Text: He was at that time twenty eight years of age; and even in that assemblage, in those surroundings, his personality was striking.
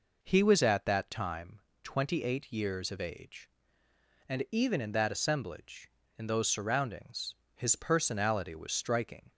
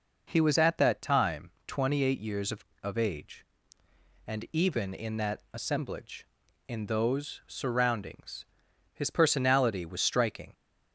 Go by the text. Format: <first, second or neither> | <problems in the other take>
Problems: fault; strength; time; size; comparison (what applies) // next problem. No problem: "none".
first | pauses between "time" and "twenty"; slight; at 1.4 s; 0.18 s long; slight in the first // says "of" twice; at 2.8 s